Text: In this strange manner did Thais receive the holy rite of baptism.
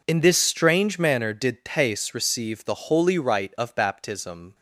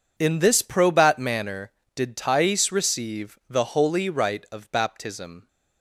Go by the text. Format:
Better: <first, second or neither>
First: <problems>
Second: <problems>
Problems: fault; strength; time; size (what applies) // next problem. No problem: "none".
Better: first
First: none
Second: says "probat" for "strange"; at 0.6 s